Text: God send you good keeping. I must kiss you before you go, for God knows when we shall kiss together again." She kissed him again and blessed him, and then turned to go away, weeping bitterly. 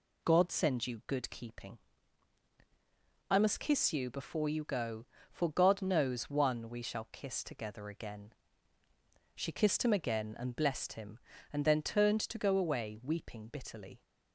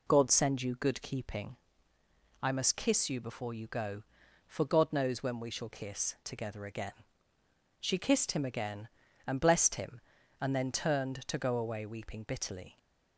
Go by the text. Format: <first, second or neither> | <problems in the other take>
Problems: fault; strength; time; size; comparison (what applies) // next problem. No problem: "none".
second | says "one" for "when"; at 6.2 s